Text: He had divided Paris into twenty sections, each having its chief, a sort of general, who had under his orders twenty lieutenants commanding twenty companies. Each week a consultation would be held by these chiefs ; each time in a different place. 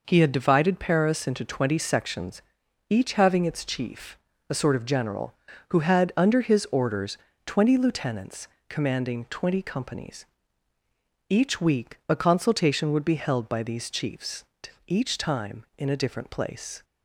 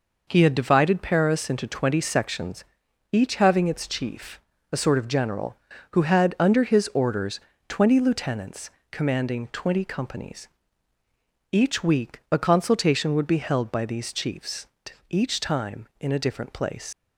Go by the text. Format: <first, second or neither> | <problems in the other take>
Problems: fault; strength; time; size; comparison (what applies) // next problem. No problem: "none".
first | pauses between "orders" and "twenty"; slight; at 7.4 s; 0.26 s long; slight in the first // pauses between "lieutenants" and "commanding"; slight; at 8.6 s; 0.22 s long; slight in the first // leaves "place" unfinished; at 16.9 s; 135 ms